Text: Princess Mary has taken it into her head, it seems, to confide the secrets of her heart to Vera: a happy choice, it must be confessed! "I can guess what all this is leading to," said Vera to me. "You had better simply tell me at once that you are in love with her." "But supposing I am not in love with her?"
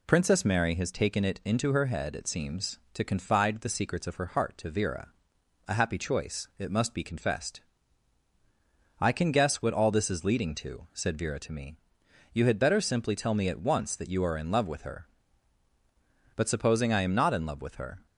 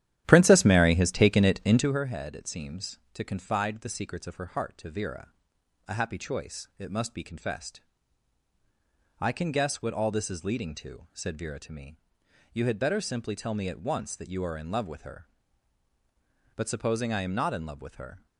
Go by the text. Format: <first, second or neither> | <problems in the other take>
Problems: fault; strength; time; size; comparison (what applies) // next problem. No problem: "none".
first | starts louder than the rest; strong; until 2.0 s; 12 dB